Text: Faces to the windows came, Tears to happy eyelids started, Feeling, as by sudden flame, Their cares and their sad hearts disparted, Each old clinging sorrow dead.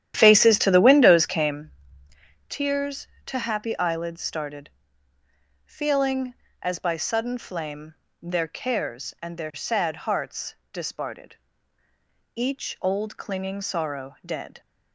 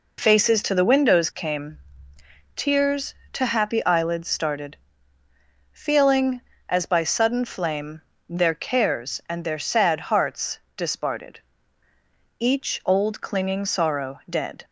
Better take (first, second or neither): second